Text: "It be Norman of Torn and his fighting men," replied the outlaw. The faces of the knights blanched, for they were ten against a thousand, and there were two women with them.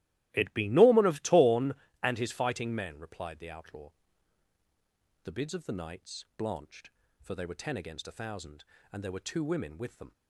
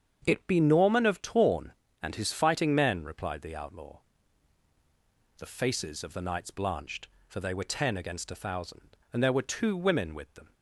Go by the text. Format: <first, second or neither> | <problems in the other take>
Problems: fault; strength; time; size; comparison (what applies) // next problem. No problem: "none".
second | starts louder than the rest; strong; until 1.3 s; 15 dB; strong in the second // says "bids" for "faces"; at 5.3 s